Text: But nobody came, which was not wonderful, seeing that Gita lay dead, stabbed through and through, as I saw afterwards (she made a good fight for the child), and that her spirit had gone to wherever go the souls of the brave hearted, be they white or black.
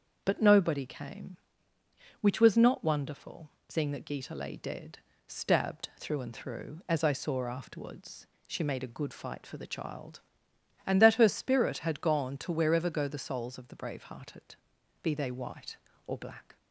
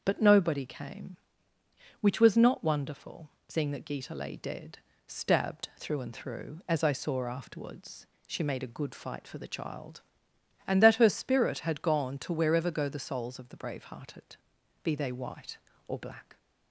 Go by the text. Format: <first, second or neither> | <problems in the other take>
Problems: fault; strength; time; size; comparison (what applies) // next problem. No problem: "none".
neither | starts louder than the rest; the same in both